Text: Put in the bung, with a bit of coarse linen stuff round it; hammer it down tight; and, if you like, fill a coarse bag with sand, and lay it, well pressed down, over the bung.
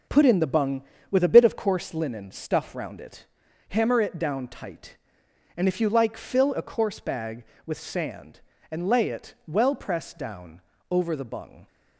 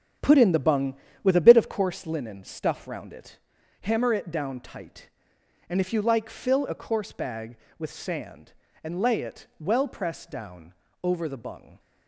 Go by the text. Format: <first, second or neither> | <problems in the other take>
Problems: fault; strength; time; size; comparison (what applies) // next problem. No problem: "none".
first | starts louder than the rest; strong; until 1.9 s; 8 dB